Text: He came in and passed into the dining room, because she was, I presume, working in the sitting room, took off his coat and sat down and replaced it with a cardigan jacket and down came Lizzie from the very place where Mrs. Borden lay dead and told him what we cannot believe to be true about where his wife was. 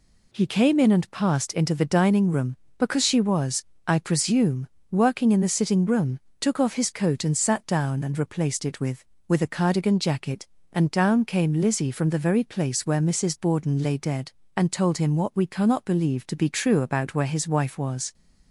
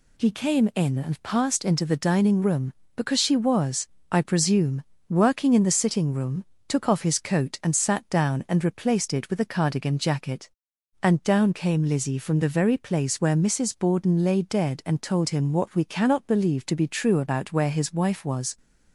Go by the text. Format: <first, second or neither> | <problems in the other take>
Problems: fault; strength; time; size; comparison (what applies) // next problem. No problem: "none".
second | says "with" twice; at 9.2 s